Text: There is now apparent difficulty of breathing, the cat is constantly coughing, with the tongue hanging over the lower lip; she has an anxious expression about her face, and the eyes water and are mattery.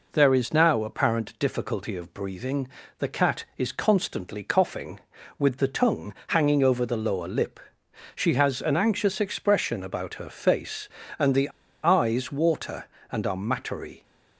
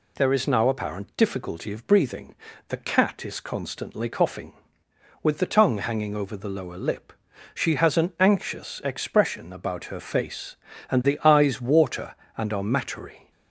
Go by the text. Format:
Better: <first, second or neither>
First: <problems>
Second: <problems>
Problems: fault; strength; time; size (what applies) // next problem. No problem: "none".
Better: second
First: pauses between "tongue" and "hanging"; slight; at 6.1 s; 0.16 s long // pauses between "the" and "eyes"; slight; at 11.4 s; 0.34 s long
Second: none